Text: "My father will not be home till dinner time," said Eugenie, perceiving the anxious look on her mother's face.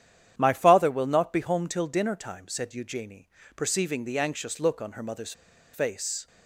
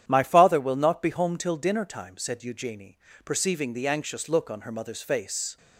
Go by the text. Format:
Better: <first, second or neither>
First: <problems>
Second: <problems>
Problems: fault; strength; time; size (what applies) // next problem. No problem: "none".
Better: second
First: starts louder than the rest; strong; until 1.3 s; 9.5 dB // pauses between "mother's" and "face"; at 5.3 s; 0.41 s long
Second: starts louder than the rest; strong; until 1.1 s; 10 dB